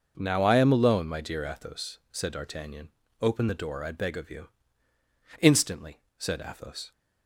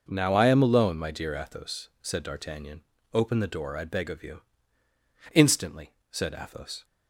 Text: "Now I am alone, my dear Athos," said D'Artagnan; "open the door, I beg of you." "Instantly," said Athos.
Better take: neither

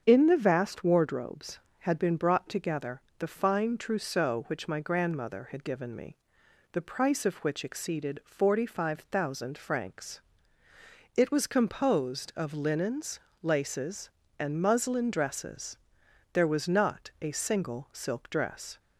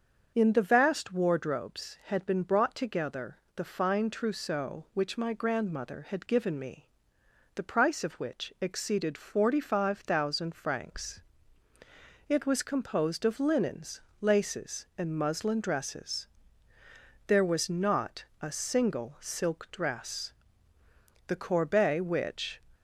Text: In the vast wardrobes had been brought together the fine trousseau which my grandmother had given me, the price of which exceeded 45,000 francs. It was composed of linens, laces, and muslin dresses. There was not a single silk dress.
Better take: first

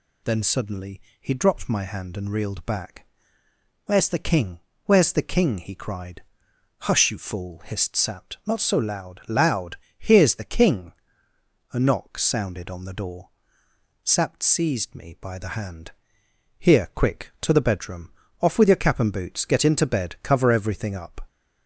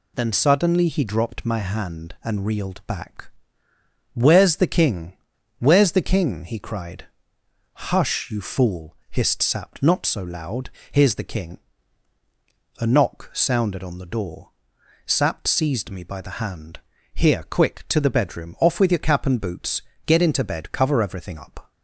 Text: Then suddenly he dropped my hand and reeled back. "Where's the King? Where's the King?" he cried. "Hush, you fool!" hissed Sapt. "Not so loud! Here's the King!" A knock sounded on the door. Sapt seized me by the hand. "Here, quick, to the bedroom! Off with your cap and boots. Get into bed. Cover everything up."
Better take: second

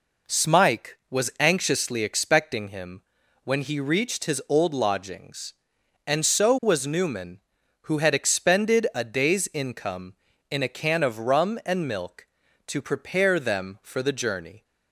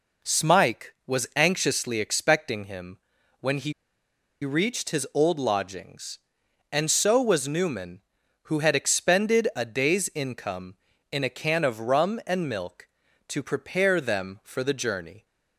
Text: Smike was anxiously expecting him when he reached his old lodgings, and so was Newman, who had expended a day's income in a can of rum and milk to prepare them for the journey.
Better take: first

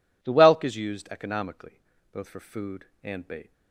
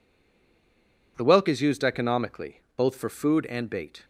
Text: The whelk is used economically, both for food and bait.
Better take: first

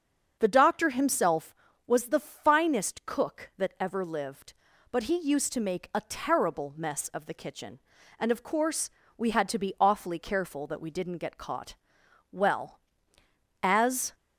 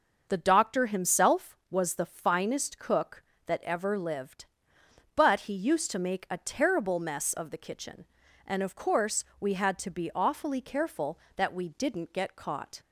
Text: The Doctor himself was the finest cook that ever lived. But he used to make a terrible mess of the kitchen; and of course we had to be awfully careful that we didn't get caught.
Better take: second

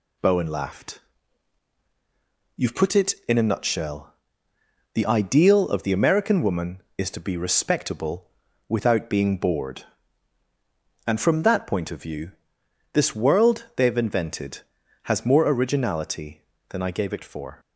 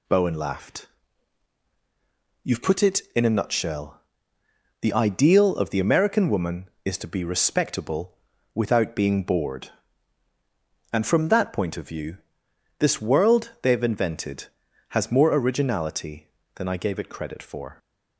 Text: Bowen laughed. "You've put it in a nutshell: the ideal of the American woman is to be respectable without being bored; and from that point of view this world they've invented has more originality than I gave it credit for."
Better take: second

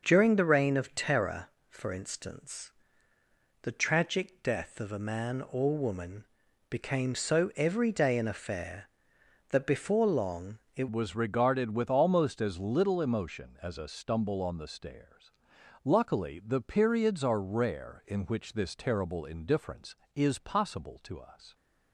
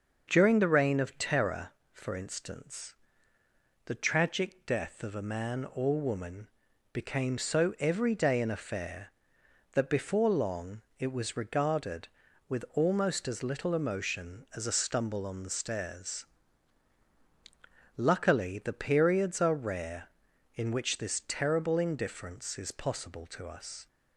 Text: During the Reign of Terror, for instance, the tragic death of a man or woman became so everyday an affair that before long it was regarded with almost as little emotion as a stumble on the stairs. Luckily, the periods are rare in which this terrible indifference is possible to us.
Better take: second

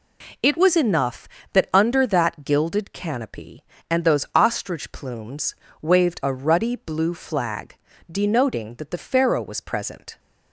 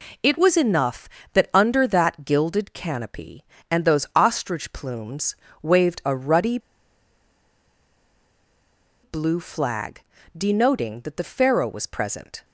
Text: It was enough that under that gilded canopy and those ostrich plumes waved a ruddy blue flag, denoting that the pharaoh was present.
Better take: first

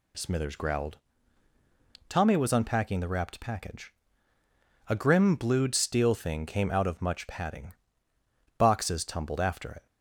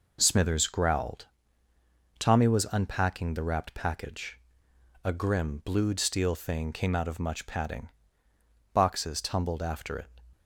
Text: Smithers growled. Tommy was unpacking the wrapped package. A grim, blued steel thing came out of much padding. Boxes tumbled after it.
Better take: neither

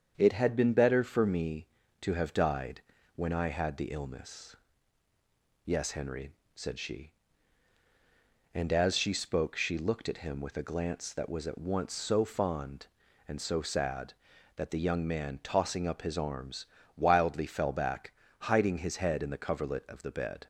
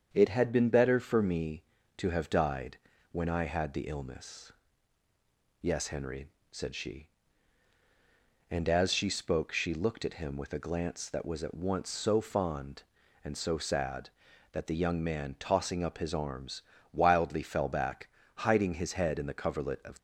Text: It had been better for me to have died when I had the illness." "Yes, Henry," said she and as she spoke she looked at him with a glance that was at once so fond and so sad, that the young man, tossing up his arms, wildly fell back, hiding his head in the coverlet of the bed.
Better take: first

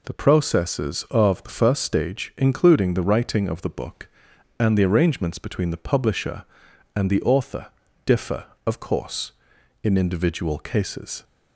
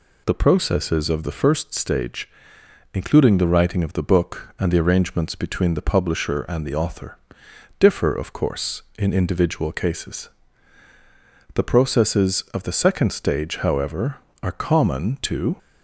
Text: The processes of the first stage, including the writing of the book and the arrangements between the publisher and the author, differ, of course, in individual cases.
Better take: first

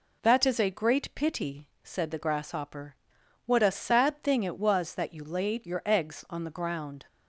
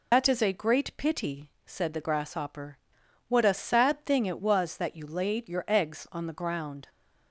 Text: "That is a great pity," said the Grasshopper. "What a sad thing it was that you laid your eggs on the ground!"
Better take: first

